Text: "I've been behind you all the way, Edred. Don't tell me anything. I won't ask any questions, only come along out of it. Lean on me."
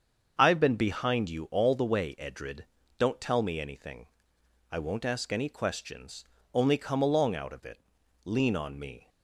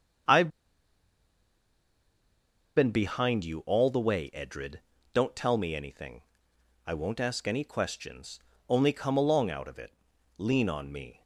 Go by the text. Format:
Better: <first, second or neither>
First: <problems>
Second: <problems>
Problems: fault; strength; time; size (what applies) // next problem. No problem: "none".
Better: first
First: starts louder than the rest; until 1.3 s; 7 dB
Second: starts louder than the rest; until 3.5 s; 7 dB // pauses between "I've" and "been"; strong; at 0.4 s; 2.2 s long